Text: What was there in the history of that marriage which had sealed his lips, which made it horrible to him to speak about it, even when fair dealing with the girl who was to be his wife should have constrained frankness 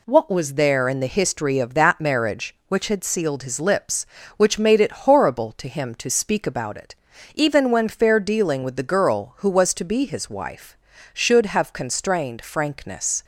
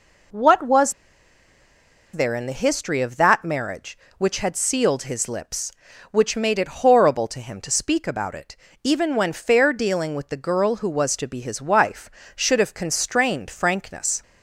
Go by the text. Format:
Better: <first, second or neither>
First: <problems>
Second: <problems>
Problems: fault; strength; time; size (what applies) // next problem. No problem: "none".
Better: first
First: none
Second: pauses between "was" and "there"; at 0.9 s; 1.2 s long